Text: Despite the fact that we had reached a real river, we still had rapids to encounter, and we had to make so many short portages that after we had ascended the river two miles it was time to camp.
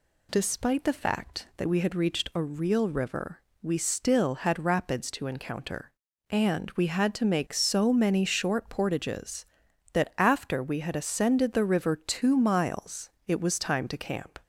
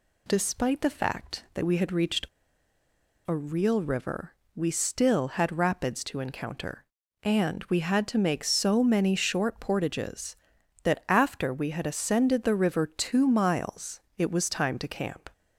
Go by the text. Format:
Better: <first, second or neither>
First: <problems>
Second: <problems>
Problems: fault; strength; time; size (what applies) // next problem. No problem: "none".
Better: first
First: pauses between "miles" and "it"; slight; at 13.1 s; 0.16 s long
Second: pauses between "reached" and "a"; at 2.2 s; 1.0 s long // pauses between "miles" and "it"; slight; at 14.0 s; 0.16 s long